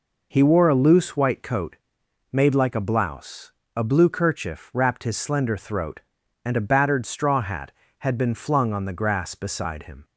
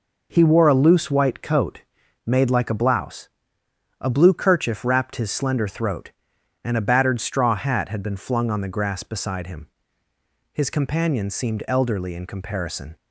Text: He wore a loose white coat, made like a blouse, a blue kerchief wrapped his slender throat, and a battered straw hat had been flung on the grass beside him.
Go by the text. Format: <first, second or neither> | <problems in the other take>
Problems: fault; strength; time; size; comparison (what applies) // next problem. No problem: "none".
first | goes on to say "His companion seemed elderly in comparison"; strong; from 10.5 s on; 2.4 s long